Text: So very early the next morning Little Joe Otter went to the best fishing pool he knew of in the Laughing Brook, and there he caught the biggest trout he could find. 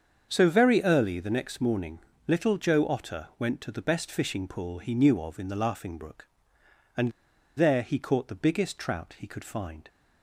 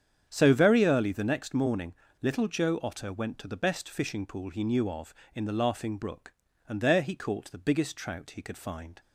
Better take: second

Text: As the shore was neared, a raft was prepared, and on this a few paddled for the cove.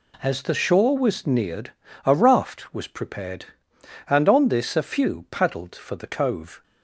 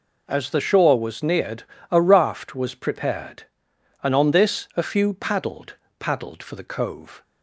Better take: first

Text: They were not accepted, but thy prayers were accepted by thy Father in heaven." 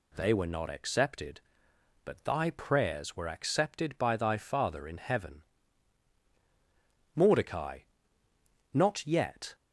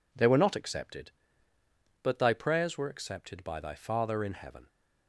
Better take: second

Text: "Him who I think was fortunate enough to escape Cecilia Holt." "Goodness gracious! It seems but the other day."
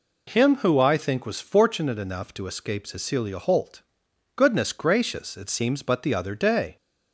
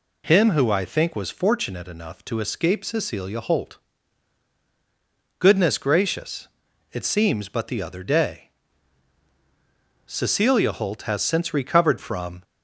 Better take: first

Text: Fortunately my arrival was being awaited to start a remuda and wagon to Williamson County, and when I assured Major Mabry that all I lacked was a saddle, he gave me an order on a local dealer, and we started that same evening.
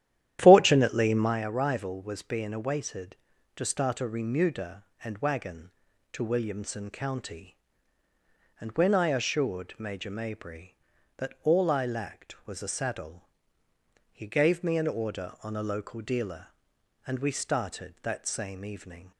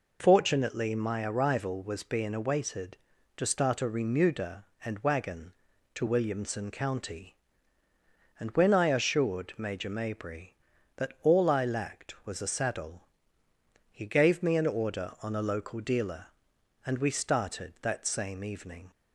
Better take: second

